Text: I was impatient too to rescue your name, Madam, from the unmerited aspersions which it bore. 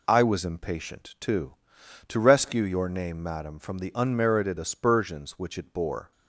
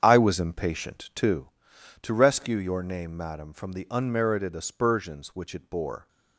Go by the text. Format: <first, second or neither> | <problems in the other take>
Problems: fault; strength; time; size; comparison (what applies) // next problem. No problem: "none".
first | starts louder than the rest; strong; until 1.4 s; 8 dB